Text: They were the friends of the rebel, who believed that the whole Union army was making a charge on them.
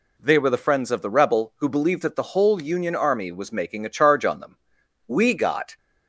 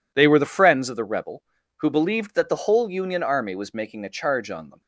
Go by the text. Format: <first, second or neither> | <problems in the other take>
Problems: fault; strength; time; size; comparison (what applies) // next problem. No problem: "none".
second | goes on to say "We got"; noticeable; from 5.0 s on; 0.70 s long